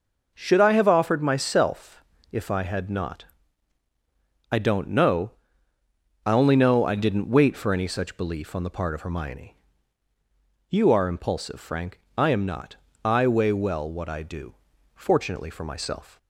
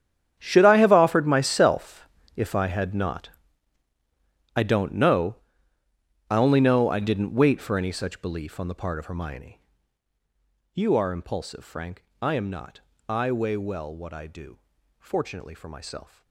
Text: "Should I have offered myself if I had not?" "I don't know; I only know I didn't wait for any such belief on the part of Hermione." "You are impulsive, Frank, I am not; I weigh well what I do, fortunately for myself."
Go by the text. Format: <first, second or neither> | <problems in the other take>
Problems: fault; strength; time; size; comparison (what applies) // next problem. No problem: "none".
first | gets quieter; strong; throughout; 16.5 dB // pauses between "myself" and "if"; slight; at 2.0 s; 0.28 s long; slight in the first